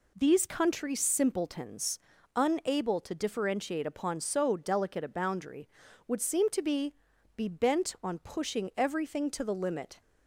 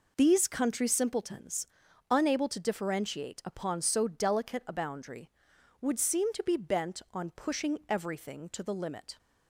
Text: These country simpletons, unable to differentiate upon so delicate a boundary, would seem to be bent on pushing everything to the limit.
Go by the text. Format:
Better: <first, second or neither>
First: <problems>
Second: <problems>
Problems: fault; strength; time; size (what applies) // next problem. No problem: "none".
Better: second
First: says "be" twice; at 7.3 s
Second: none